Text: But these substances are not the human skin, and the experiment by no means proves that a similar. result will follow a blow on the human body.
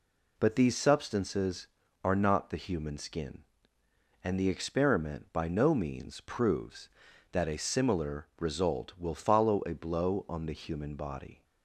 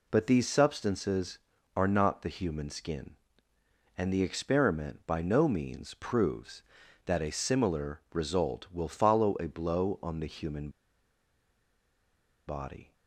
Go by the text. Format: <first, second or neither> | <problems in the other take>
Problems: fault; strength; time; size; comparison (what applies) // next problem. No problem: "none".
first | pauses between "human" and "body"; strong; at 10.6 s; 1.7 s long